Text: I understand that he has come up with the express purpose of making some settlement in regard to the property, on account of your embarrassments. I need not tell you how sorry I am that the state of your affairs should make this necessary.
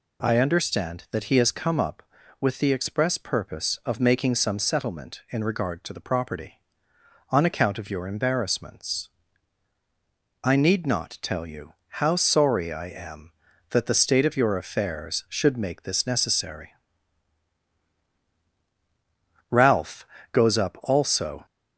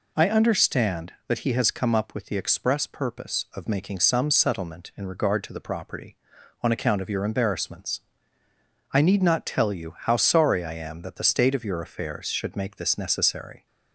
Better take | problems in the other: second | goes on to say "Ralph goes up also"; strong; from 19.4 s on; 1.9 s long

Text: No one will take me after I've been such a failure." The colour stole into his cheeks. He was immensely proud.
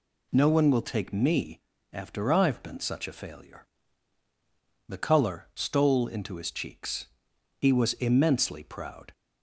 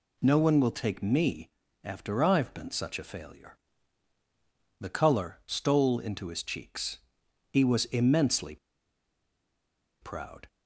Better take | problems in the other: first | pauses between "me" and "after"; slight; at 1.4 s; 0.34 s long; slight in the first // pauses between "immensely" and "proud"; strong; at 8.5 s; 1.4 s long

